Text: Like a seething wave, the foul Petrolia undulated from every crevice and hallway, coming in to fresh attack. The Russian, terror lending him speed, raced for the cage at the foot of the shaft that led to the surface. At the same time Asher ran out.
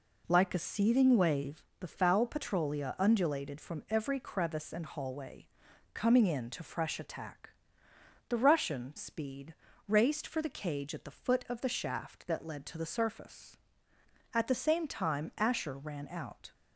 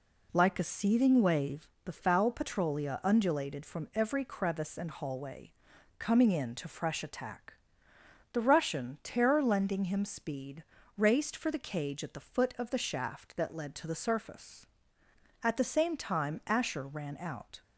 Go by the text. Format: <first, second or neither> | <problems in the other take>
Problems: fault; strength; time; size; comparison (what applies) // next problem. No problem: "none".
second | skips "terror lending him"; at 8.9 s